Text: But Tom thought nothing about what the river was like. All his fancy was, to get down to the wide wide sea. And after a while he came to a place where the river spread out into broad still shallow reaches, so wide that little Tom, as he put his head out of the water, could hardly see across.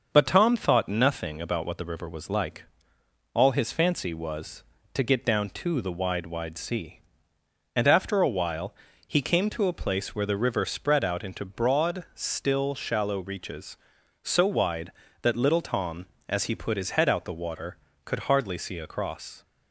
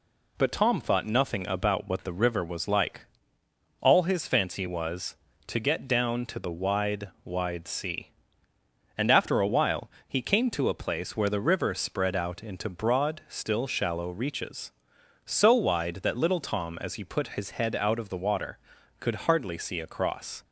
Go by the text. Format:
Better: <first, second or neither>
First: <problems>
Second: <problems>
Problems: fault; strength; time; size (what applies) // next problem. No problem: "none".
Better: second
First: starts louder than the rest; until 1.1 s; 6.5 dB // pauses between "while" and "he"; slight; at 8.7 s; 0.32 s long // skips "of"; at 17.2 s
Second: pauses between "while" and "he"; slight; at 9.8 s; 0.18 s long